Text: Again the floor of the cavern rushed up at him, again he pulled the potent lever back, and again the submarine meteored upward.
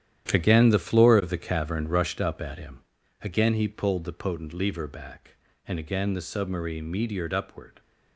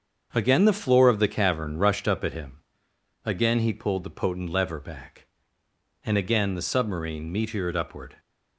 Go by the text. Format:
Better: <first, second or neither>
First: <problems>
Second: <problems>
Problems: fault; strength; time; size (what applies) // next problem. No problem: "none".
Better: second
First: gets quieter; strong; throughout; 10.5 dB // starts louder than the rest; strong; until 1.3 s; 10.5 dB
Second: starts louder than the rest; until 1.3 s; 7 dB